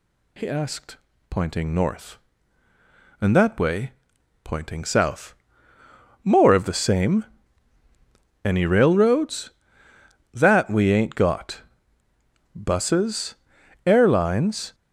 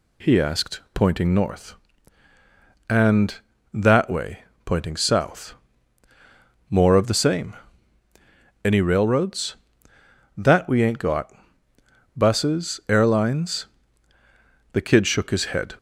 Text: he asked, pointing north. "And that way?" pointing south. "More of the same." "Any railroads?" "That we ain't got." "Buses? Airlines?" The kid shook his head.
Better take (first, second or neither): second